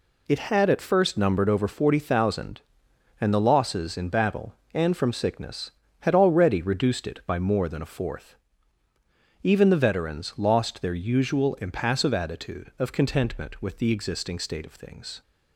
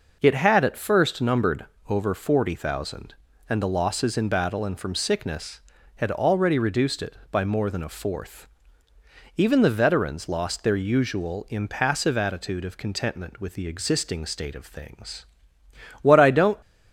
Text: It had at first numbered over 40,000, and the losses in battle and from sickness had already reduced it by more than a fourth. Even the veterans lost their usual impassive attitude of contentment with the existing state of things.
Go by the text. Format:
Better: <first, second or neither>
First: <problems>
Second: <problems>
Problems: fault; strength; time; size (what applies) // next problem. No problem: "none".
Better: first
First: none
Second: pauses between "numbered" and "over"; slight; at 1.6 s; 0.22 s long // goes on to say "What I don't"; from 16.0 s on; 0.56 s long